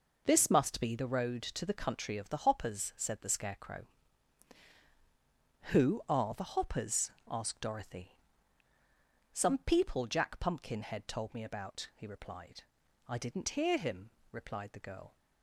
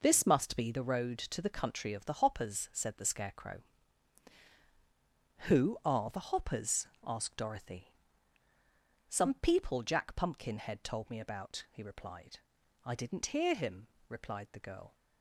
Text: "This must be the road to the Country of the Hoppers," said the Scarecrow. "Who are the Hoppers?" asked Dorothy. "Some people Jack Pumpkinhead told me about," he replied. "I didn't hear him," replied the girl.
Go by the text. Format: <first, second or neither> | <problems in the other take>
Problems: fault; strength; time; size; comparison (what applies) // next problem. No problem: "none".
neither | none